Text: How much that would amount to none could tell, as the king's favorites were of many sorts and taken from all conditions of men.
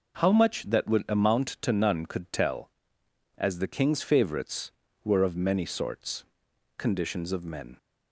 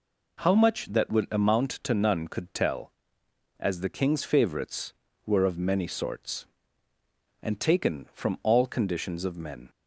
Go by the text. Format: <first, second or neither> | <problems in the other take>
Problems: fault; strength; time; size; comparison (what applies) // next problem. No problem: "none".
second | starts louder than the rest; until 1.3 s; 6.5 dB // skips "and taken from all"; at 6.5 s